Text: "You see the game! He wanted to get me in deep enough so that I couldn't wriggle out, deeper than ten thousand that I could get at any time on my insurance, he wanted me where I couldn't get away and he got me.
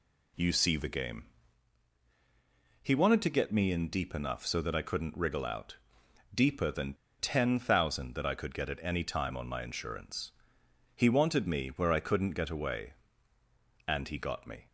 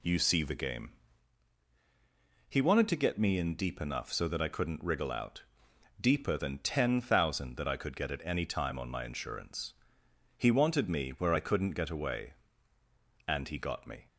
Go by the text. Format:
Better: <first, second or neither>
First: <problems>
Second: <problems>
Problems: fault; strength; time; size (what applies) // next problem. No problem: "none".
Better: second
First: pauses between "than" and "ten"; slight; at 6.9 s; 0.25 s long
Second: none